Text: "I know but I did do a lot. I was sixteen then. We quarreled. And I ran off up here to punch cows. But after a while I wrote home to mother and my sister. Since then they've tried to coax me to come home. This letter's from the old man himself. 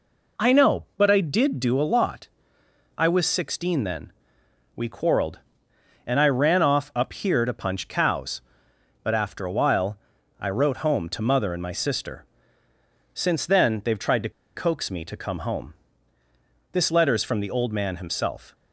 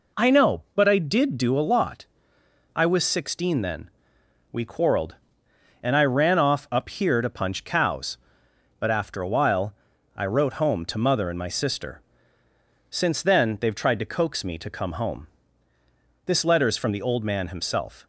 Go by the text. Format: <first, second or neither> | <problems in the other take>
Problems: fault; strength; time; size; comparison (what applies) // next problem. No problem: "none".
second | pauses between "while" and "I"; at 9.9 s; 0.40 s long; also in the second // pauses between "to" and "coax"; slight; at 14.2 s; 0.25 s long